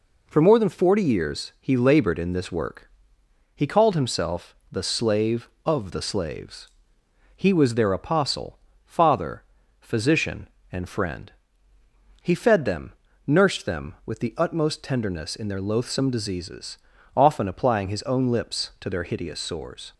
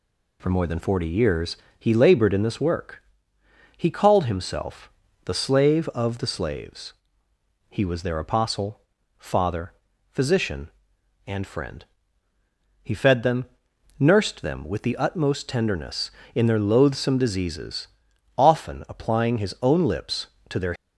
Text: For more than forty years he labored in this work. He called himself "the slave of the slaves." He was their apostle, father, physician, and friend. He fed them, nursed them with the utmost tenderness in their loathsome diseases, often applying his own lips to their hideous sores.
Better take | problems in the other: first | pauses between "years" and "he"; slight; at 1.5 s; 0.24 s long // pauses between "himself" and "the"; slight; at 4.8 s; 0.36 s long; slight in the first // stops before "hideous sores"; at 20.7 s

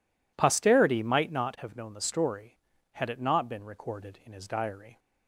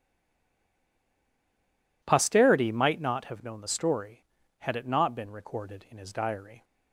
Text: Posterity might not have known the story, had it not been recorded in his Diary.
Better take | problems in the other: first | stays silent before the first word; noticeable; until 2.0 s; 2.0 s long

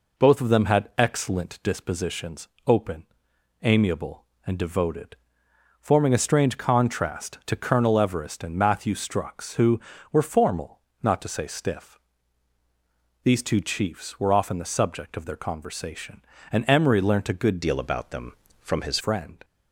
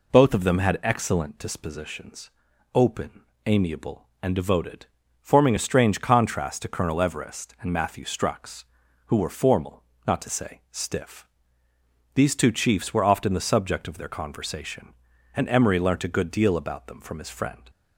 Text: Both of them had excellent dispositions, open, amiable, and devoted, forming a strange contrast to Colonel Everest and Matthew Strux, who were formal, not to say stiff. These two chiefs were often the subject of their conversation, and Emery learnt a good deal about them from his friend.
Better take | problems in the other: second | changes voice from "deal" to "his"; from 17.6 to 18.9 s; 1.3 s long

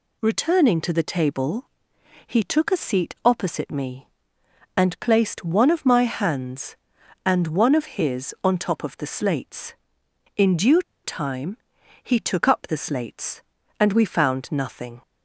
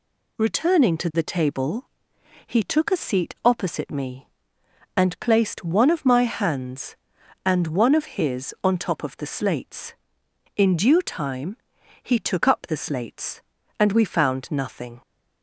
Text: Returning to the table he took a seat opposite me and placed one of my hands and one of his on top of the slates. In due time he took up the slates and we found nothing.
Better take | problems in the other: second | pauses between "table" and "he"; noticeable; at 1.6 s; 0.58 s long; noticeable in the second // pauses between "due" and "time"; slight; at 10.8 s; 0.23 s long // pauses between "time" and "he"; at 11.5 s; 0.44 s long; also in the second

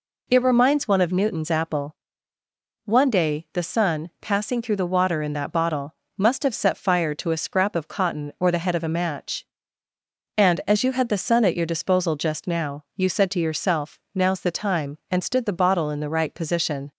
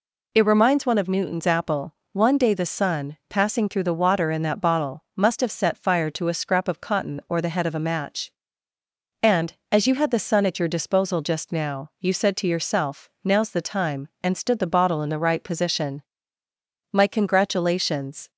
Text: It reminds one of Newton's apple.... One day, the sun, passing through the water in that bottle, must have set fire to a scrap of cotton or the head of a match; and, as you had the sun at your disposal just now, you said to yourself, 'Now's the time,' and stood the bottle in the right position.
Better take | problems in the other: first | goes on to say "My congratulations"; from 16.9 s on; 1.3 s long

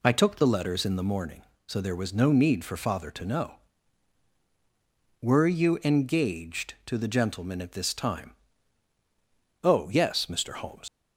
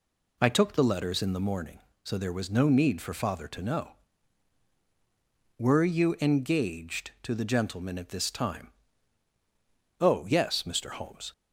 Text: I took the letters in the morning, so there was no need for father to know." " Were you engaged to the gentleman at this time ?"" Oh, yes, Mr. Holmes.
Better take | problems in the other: second | leaves "Holmes" unfinished; at 10.8 s; 70 ms

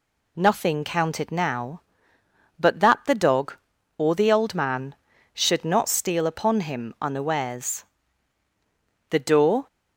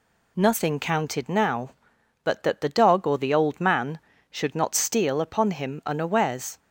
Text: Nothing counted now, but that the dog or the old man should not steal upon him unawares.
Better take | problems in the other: second | goes on to say "The door"; from 9.0 s on; 0.58 s long

